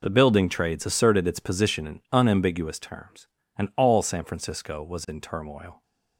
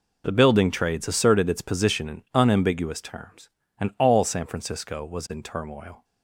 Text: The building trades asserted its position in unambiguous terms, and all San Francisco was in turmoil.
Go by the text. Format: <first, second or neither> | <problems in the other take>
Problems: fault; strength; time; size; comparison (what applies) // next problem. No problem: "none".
neither | none